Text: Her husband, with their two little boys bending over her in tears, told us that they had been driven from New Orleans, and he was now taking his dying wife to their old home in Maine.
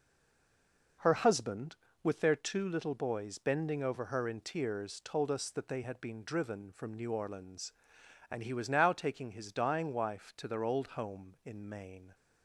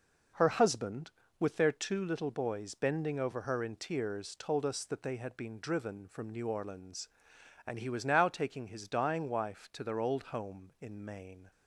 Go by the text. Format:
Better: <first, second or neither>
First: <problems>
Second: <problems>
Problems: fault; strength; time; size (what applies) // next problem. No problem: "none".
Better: second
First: stays silent before the first word; until 1.0 s; 1.0 s long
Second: none